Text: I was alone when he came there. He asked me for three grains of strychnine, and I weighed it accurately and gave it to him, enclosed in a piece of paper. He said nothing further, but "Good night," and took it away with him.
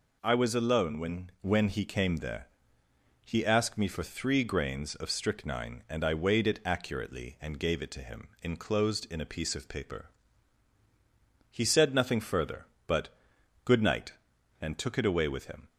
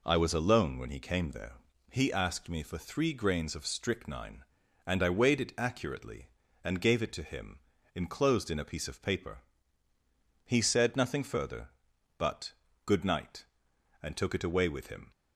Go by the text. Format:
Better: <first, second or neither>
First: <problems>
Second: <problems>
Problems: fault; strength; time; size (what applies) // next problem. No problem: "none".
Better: second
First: says "when" twice; at 1.4 s // pauses between "but" and "Good"; noticeable; at 13.0 s; 0.56 s long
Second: pauses between "but" and "Good"; slight; at 12.5 s; 0.34 s long